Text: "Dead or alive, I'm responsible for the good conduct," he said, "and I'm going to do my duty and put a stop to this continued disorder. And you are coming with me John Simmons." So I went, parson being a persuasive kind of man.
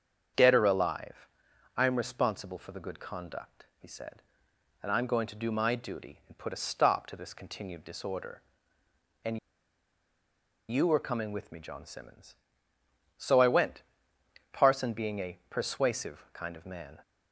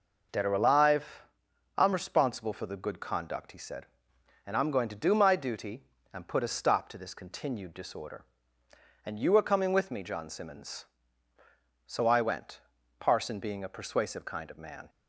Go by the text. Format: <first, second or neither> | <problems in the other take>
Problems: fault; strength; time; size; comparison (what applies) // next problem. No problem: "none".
second | starts louder than the rest; strong; until 1.8 s; 7.5 dB // pauses between "And" and "you"; strong; at 9.3 s; 1.3 s long